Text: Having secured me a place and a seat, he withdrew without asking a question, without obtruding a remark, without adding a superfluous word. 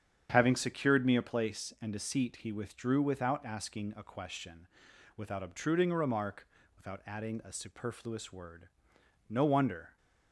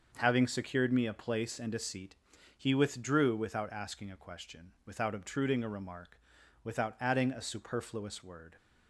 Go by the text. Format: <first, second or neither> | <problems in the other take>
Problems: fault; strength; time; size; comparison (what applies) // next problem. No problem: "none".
second | starts louder than the rest; strong; until 1.3 s; 8 dB; also in the second // goes on to say "No wonder"; noticeable; from 9.2 s on; 0.68 s long